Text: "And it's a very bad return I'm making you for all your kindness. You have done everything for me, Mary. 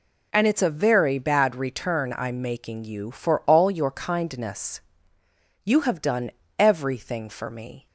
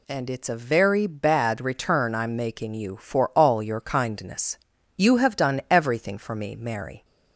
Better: second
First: pauses between "done" and "everything"; slight; at 6.3 s; 0.26 s long // stops before "Mary"; at 7.8 s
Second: none

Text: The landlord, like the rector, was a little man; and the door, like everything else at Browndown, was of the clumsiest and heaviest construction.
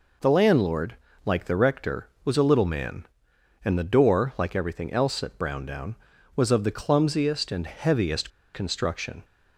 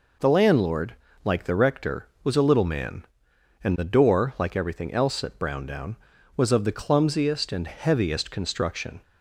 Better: second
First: pauses between "heaviest" and "construction"; slight; at 8.3 s; 0.24 s long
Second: none

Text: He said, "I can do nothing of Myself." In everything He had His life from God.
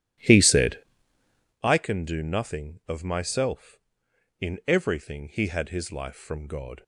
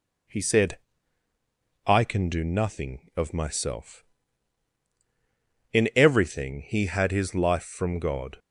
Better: second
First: starts louder than the rest; strong; until 1.6 s; 13 dB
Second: none

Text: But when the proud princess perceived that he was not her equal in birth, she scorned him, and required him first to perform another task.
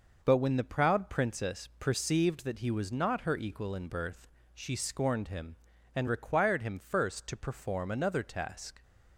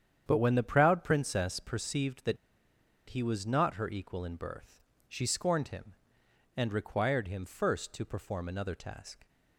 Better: first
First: none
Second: starts louder than the rest; strong; until 1.2 s; 9 dB // pauses between "that" and "he"; noticeable; at 2.3 s; 0.73 s long

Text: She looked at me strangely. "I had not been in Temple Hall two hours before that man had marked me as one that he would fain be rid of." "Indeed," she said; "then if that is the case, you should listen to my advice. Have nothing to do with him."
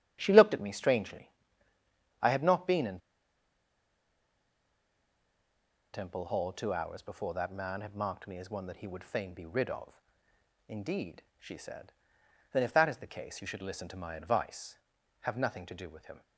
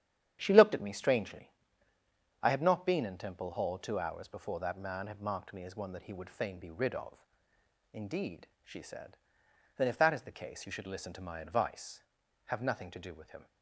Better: second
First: starts louder than the rest; strong; until 1.2 s; 9.5 dB // pauses between "in" and "Temple"; strong; at 2.9 s; 2.9 s long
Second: starts louder than the rest; strong; until 1.4 s; 9.5 dB

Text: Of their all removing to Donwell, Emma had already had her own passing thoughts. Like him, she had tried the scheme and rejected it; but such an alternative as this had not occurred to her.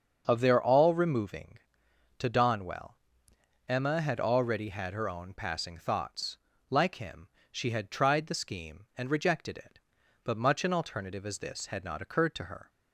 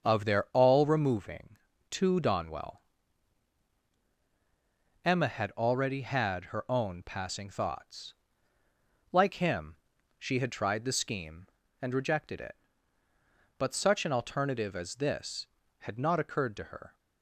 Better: second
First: starts louder than the rest; until 1.2 s; 7 dB // says "much" for "such"; at 10.3 s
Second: starts louder than the rest; strong; until 1.1 s; 7 dB

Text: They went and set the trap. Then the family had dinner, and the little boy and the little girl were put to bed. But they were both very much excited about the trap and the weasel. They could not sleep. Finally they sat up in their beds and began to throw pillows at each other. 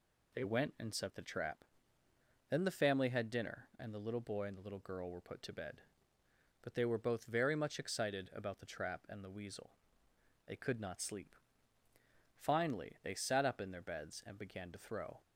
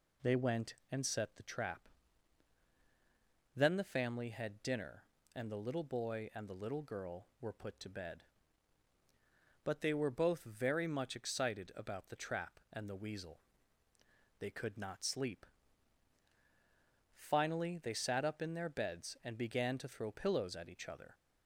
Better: second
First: stops before "pillows at each other"; at 15.2 s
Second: none

